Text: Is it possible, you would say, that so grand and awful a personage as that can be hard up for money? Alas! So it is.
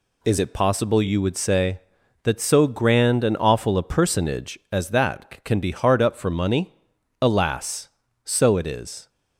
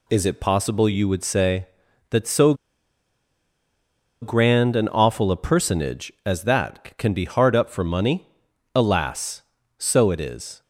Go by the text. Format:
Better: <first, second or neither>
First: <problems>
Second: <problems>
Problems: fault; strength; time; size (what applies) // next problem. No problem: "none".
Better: first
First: none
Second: pauses between "so" and "grand"; strong; at 2.5 s; 1.6 s long